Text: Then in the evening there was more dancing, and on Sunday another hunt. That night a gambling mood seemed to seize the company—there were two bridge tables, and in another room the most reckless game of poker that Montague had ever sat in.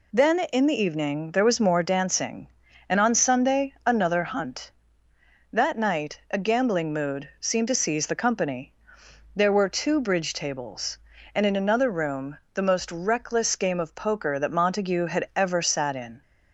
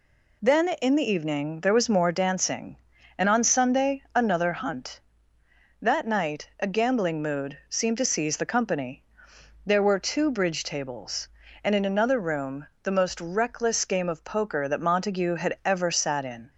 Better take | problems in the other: neither | pauses between "room" and "the"; slight; the same in both

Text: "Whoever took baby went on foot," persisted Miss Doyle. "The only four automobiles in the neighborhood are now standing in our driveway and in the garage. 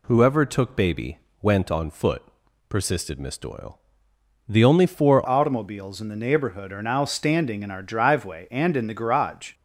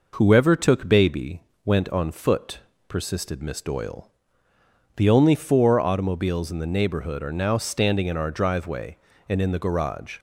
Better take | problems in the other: second | pauses between "baby" and "went"; slight; at 1.1 s; 0.24 s long; slight in the second // changes voice at "automobiles"; from 5.2 s on; 4.3 s long

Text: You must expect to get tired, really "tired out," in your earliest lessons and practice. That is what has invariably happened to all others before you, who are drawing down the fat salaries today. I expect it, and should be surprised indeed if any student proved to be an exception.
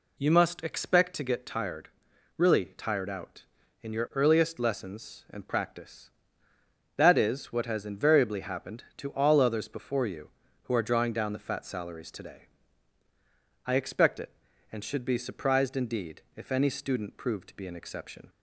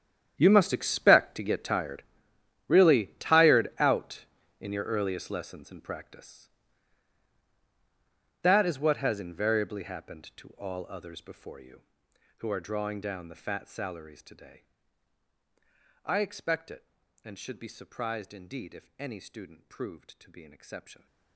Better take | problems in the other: first | gets quieter; strong; throughout; 18 dB

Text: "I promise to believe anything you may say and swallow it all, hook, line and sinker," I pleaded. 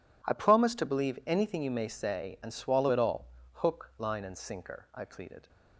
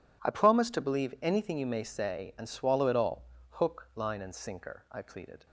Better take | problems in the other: neither | none

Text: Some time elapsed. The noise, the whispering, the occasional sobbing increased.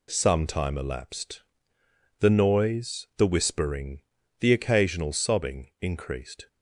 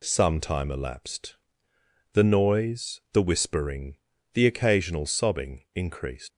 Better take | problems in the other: first | leaves "increased" unfinished; at 6.3 s; 110 ms

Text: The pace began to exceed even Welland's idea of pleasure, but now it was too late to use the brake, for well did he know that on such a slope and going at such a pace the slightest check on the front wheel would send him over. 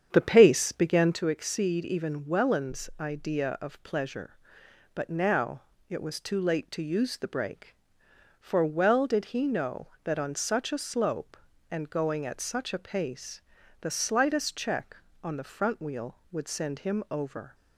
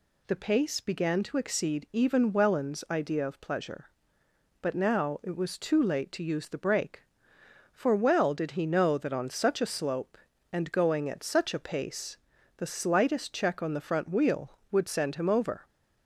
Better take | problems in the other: second | starts louder than the rest; strong; until 1.3 s; 8 dB // pauses between "now" and "it"; slight; at 5.6 s; 0.26 s long // pauses between "pace" and "the"; at 13.4 s; 0.42 s long; also in the second

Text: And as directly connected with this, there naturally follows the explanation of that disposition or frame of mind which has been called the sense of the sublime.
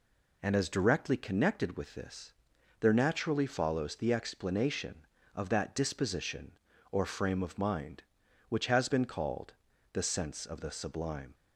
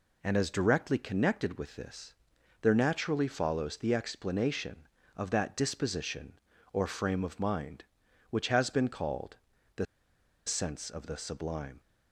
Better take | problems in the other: first | pauses between "called" and "the"; at 9.3 s; 0.40 s long; also in the first // pauses between "the" and "sense"; noticeable; at 9.8 s; 0.61 s long

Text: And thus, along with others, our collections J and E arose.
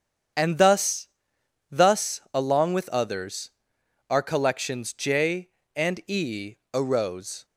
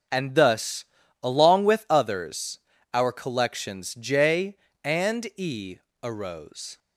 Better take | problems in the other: second | starts louder than the rest; strong; until 1.9 s; 8 dB; also in the second // says "thus" twice; at 1.6 s // pauses between "E" and "arose"; slight; at 6.5 s; 0.18 s long; slight in the second

